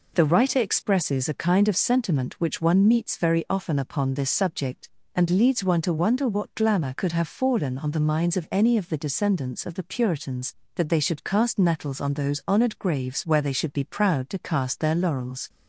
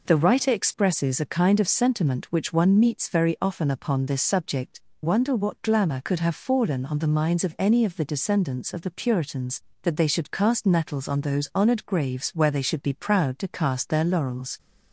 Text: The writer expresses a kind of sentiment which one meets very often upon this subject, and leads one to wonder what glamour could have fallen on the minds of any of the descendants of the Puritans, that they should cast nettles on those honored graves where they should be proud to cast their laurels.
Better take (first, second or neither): first